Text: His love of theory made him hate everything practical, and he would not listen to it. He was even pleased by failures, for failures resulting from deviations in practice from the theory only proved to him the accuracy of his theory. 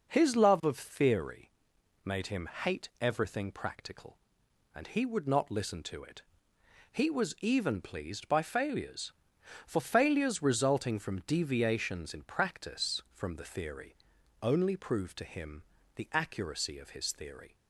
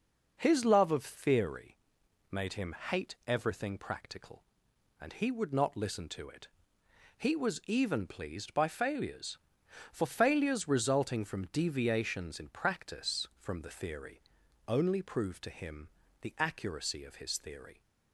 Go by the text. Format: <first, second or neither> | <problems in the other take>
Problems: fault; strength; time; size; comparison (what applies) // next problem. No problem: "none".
neither | pauses between "theory" and "made"; noticeable; the same in both // pauses between "theory" and "only"; noticeable; the same in both // pauses between "him" and "the"; slight; the same in both